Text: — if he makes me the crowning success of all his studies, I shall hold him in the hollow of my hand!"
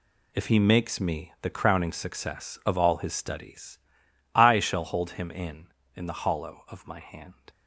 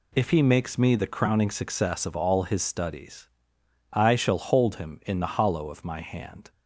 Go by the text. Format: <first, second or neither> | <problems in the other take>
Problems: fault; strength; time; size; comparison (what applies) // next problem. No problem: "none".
second | says "in" twice; at 5.9 s